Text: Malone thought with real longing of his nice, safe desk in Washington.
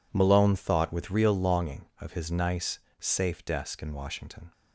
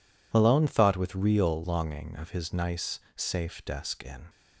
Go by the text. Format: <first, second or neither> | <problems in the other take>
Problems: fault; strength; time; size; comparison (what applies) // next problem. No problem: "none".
first | stops before "Washington"; at 4.2 s